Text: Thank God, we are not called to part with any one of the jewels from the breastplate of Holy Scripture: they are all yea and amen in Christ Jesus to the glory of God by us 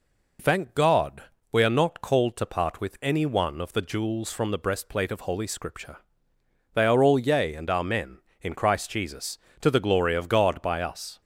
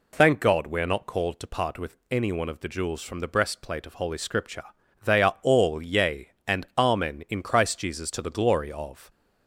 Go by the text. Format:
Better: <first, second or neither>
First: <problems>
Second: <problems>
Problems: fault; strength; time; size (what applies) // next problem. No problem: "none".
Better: first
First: none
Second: stops before "God by us"; at 9.0 s